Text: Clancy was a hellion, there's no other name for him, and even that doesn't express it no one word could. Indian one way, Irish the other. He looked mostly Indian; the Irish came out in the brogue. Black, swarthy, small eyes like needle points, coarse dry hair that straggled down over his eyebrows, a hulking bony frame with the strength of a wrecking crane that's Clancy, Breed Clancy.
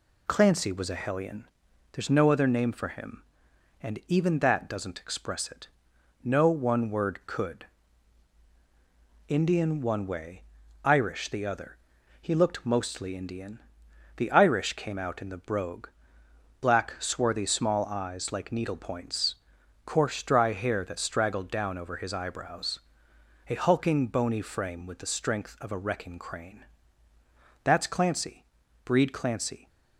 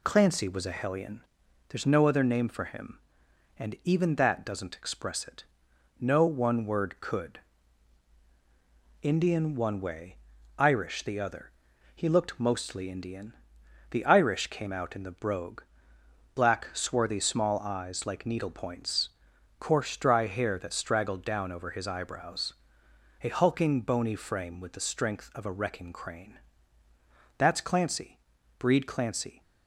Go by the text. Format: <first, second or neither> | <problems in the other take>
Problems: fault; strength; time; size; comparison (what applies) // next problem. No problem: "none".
neither | pauses between "it" and "no"; noticeable; the same in both // pauses between "crane" and "that's"; the same in both